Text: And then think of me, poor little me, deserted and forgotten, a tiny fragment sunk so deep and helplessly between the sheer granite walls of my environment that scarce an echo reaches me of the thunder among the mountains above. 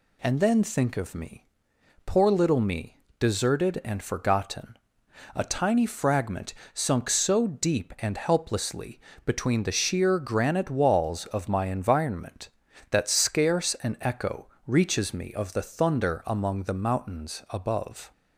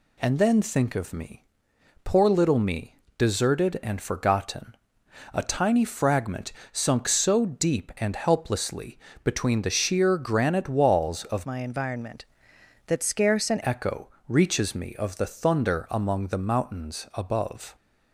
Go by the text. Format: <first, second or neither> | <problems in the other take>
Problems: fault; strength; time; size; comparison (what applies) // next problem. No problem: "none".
first | pauses between "fragment" and "sunk"; slight; at 6.5 s; 0.18 s long; slight in the first // pauses between "helplessly" and "between"; slight; at 8.9 s; 0.26 s long; slight in the first // changes voice from "my" to "an"; from 11.4 to 13.6 s; 2.2 s long // pauses between "echo" and "reaches"; slight; at 14.0 s; 0.18 s long; slight in the first